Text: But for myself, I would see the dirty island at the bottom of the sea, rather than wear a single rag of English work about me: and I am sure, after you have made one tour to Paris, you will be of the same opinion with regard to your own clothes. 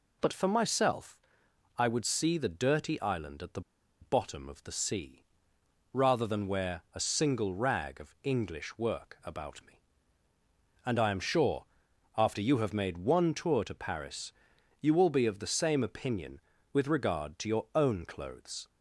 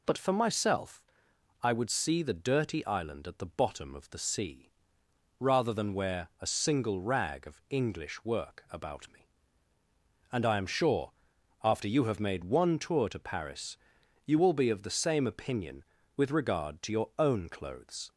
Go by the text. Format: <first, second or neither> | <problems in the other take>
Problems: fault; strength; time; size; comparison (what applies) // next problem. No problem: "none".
second | pauses between "the" and "bottom"; at 3.6 s; 0.40 s long